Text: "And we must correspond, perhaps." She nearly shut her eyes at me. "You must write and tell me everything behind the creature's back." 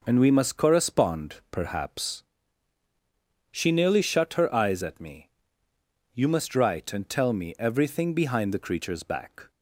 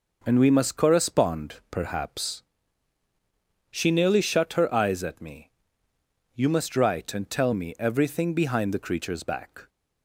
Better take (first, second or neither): neither